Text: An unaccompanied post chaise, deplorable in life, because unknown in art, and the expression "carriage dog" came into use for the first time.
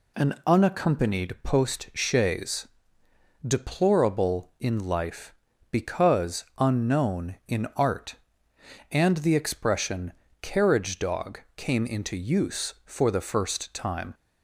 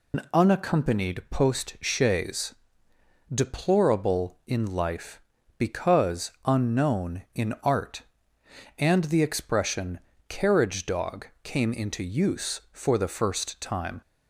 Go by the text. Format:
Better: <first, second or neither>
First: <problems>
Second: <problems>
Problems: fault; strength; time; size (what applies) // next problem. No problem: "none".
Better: first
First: pauses between "expression" and "carriage"; slight; at 10.1 s; 0.28 s long // pauses between "dog" and "came"; slight; at 11.3 s; 0.16 s long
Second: loses the start of "An"; at 0.1 s; 115 ms // pauses between "expression" and "carriage"; slight; at 9.9 s; 0.28 s long // pauses between "dog" and "came"; slight; at 11.2 s; 0.16 s long